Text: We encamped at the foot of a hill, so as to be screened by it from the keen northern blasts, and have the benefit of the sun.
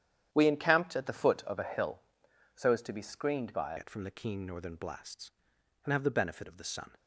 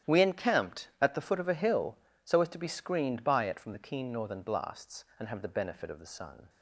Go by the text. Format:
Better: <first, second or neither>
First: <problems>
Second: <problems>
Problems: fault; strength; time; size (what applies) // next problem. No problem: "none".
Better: second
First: starts louder than the rest; strong; until 1.3 s; 9.5 dB // changes voice at "it"; from 3.7 s on; 3.2 s long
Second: starts louder than the rest; strong; until 1.1 s; 11 dB